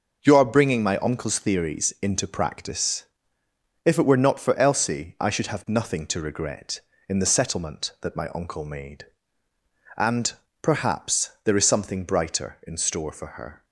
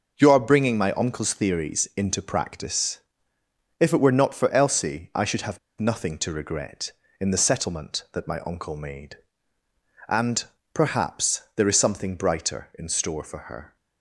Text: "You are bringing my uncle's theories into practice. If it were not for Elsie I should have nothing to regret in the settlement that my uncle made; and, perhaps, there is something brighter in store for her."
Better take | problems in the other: first | pauses between "have" and "nothing"; slight; at 5.5 s; 0.20 s long

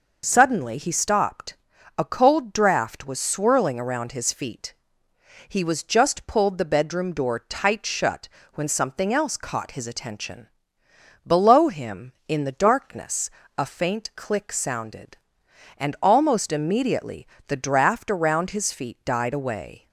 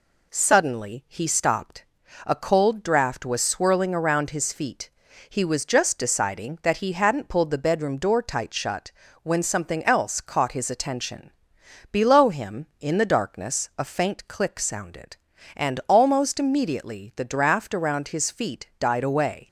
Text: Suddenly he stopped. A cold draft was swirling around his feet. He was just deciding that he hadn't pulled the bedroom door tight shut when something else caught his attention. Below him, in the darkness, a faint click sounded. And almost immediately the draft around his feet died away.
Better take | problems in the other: second | skips "deciding that he hadn't"; at 6.2 s // pauses between "shut" and "when"; slight; at 8.2 s; 0.28 s long; slight in the second // pauses between "immediately" and "the"; slight; at 17.2 s; 0.22 s long

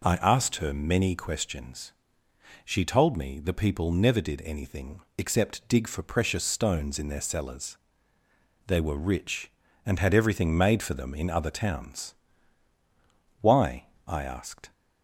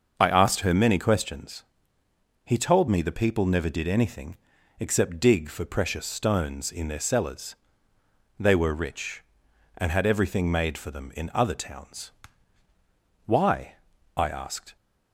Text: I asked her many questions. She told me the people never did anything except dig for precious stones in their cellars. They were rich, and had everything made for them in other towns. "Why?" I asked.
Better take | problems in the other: first | starts louder than the rest; until 1.1 s; 6.5 dB // says "He" for "She"; at 2.4 s // pauses between "anything" and "except"; at 4.3 s; 0.42 s long; slight in the first

